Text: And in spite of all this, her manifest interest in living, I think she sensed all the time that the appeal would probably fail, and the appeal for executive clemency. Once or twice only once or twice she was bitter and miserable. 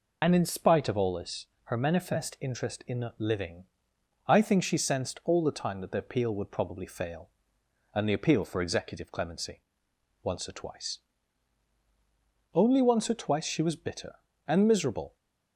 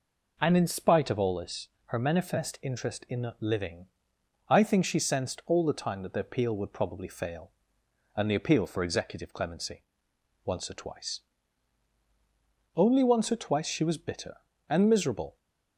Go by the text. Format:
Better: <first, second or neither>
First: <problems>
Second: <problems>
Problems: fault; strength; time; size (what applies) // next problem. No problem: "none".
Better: second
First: loses the start of "And"; at 0.2 s; 45 ms // pauses between "twice" and "only"; strong; at 10.9 s; 1.5 s long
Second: pauses between "twice" and "only"; strong; at 11.1 s; 1.5 s long